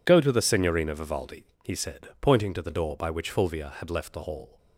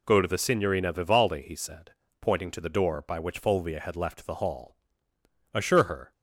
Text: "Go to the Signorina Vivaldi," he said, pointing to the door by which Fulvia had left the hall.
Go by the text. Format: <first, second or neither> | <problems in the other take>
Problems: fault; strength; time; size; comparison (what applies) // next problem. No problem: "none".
first | goes on to say "Assure her"; from 5.5 s on; 0.58 s long